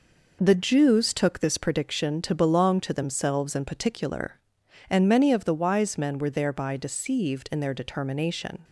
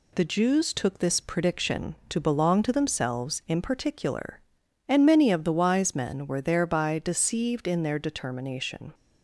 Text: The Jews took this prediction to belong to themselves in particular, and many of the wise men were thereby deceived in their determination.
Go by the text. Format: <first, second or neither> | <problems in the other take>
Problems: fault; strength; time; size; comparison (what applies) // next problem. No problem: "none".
neither | none